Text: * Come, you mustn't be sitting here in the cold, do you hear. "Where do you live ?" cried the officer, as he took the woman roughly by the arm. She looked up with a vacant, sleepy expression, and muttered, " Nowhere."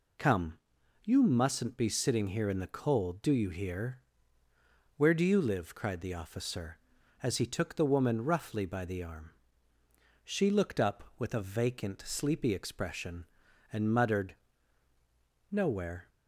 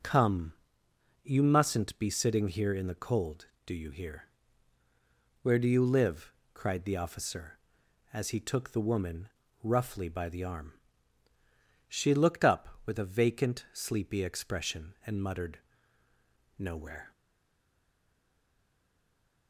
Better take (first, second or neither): first